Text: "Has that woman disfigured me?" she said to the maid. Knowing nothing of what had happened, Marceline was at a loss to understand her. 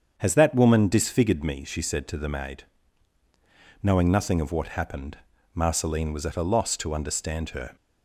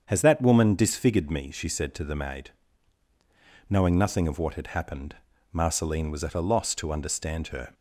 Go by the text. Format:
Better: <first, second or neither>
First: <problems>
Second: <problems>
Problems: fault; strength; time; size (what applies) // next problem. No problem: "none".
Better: second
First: starts louder than the rest; strong; until 1.1 s; 7.5 dB // skips "had"; at 4.6 s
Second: starts louder than the rest; strong; until 1.0 s; 7.5 dB